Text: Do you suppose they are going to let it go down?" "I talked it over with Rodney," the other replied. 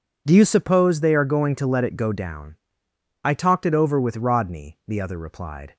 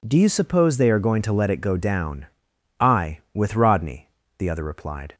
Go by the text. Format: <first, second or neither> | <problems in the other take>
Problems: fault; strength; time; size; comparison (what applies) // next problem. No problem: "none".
first | skips "talked it over"; at 3.2 s